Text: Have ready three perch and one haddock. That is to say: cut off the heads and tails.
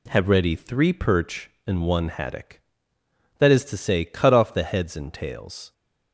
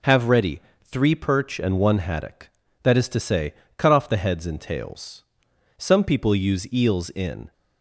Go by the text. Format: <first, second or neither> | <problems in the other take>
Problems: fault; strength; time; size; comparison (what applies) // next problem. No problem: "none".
first | pauses between "ready" and "three"; slight; at 0.6 s; 0.22 s long // goes on to say "Some people use eels in"; strong; from 5.7 s on; 1.7 s long